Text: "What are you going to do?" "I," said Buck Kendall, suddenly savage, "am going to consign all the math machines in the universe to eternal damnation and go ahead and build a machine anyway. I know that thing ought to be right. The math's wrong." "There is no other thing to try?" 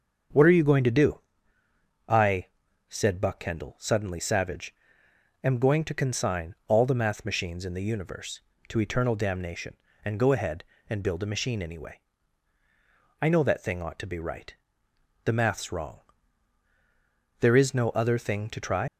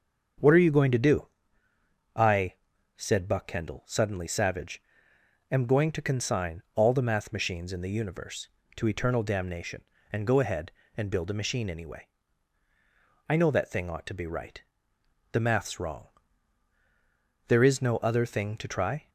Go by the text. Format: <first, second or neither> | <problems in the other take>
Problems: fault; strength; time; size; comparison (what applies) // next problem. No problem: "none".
second | starts louder than the rest; until 2.2 s; 7 dB; also in the second // leaves "try" unfinished; at 18.8 s; 135 ms